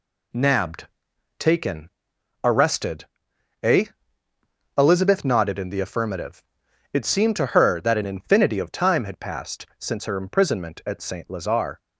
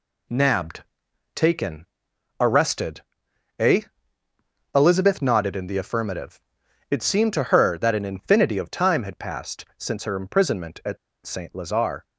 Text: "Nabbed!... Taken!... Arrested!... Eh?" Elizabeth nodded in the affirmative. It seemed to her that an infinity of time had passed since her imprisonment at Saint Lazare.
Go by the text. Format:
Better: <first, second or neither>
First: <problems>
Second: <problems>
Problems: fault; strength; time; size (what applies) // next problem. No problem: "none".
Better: first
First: none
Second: pauses between "at" and "Saint"; slight; at 10.9 s; 0.27 s long